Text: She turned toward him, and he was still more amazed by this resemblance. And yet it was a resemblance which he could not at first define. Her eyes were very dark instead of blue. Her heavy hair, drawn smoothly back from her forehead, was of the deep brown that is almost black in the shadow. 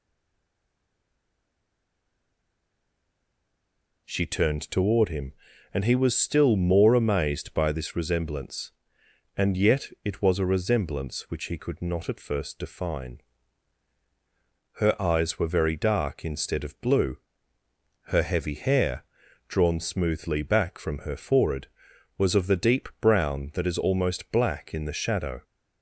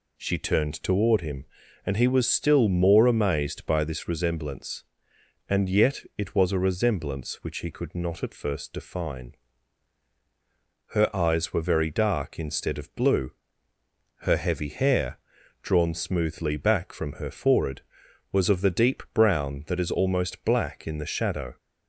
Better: second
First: stays silent before the first word; strong; until 4.0 s; 4.0 s long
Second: none

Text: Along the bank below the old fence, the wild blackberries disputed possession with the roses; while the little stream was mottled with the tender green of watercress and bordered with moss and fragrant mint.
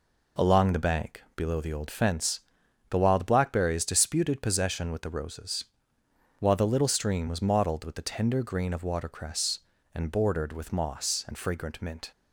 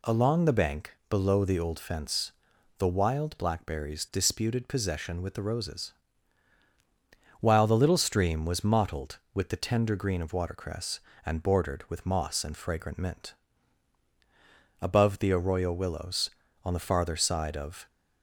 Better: first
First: none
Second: goes on to say "Above the arroyo willows on the farther side of"; strong; from 14.8 s on; 3.0 s long

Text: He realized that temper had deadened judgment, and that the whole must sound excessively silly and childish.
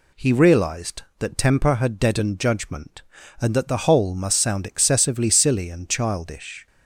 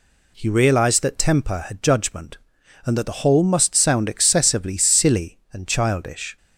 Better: first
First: none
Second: skips "deadened"; at 1.8 s

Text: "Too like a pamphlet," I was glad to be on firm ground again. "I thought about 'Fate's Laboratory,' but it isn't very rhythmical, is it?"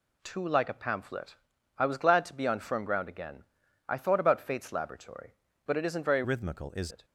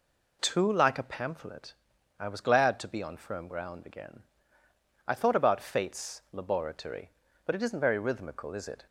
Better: second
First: changes voice from "rhythmical" to "is"; from 6.2 to 6.9 s; 0.7 s long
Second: none

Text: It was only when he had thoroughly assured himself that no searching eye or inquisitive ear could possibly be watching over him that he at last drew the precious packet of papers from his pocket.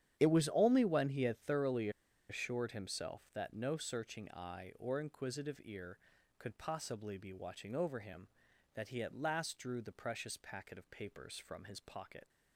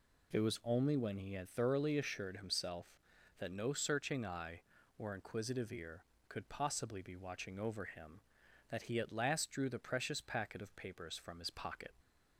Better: second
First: starts louder than the rest; strong; until 1.2 s; 10 dB // pauses between "thoroughly" and "assured"; at 1.8 s; 0.40 s long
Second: none

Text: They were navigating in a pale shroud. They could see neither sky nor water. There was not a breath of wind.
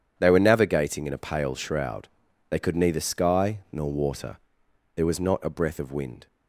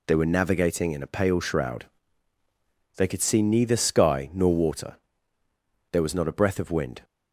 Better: second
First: skips "see"; at 2.7 s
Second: none

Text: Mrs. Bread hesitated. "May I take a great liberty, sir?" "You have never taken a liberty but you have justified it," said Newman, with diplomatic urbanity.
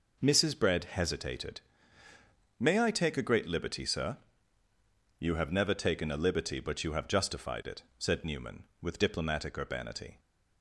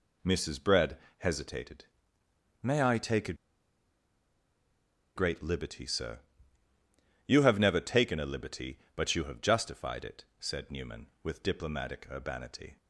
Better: first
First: none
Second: pauses between "Bread" and "hesitated"; slight; at 0.9 s; 0.22 s long // pauses between "a" and "great"; strong; at 3.3 s; 1.8 s long

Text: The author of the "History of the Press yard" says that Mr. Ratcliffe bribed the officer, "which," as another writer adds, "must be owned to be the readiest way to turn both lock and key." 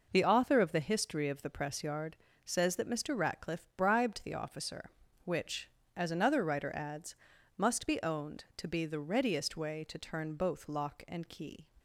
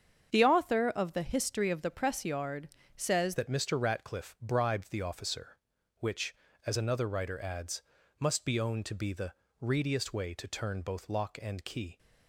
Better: first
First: pauses between "yard" and "says"; slight; at 2.1 s; 0.30 s long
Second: starts louder than the rest; strong; until 1.3 s; 7.5 dB // pauses between "yard" and "says"; slight; at 2.6 s; 0.28 s long // changes voice at "that"; from 3.3 s on; 8.6 s long // pauses between "the" and "readiest"; slight; at 9.3 s; 0.26 s long

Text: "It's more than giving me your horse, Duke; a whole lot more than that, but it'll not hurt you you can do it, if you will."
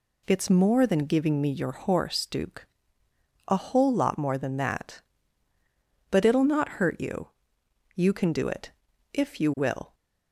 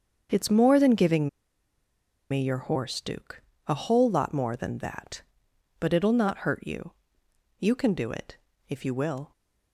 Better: first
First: pauses between "you" and "you"; noticeable; at 7.2 s; 0.66 s long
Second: starts louder than the rest; until 2.3 s; 7 dB // pauses between "giving" and "me"; at 1.2 s; 1.0 s long // pauses between "you" and "you"; noticeable; at 6.9 s; 0.66 s long

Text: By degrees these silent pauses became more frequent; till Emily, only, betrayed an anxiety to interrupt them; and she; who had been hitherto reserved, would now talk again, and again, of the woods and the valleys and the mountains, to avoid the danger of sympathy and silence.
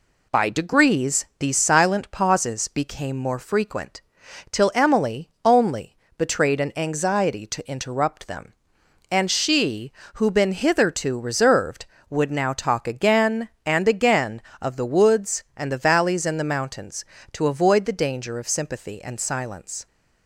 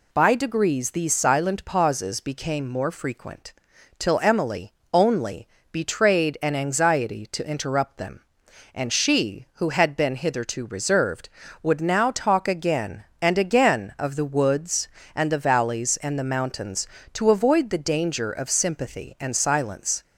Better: second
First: skips "had"; at 10.3 s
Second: none

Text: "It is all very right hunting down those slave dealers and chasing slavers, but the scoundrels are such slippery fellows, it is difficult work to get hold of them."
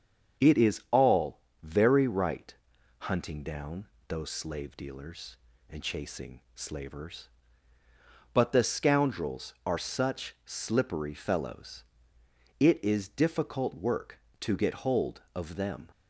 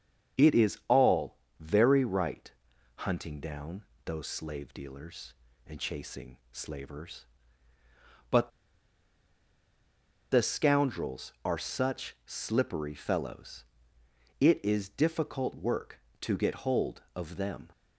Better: first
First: starts louder than the rest; until 1.7 s; 7 dB // pauses between "all" and "very"; slight; at 1.4 s; 0.22 s long // pauses between "right" and "hunting"; at 2.5 s; 0.44 s long // pauses between "down" and "those"; slight; at 3.8 s; 0.22 s long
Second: starts louder than the rest; until 1.6 s; 7 dB // pauses between "all" and "very"; slight; at 1.3 s; 0.22 s long // pauses between "right" and "hunting"; at 2.5 s; 0.44 s long // pauses between "down" and "those"; slight; at 3.8 s; 0.22 s long // pauses between "but" and "the"; strong; at 8.4 s; 1.8 s long

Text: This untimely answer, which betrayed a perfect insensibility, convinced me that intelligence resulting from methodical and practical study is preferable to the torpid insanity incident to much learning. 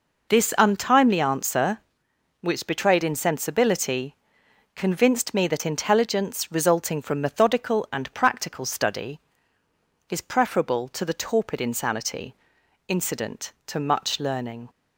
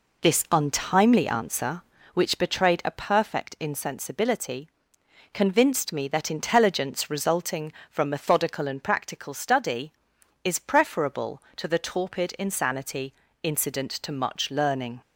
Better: second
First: skips "a perfect"; at 3.0 s // pauses between "insanity" and "incident"; noticeable; at 12.3 s; 0.54 s long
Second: pauses between "insanity" and "incident"; slight; at 13.1 s; 0.30 s long

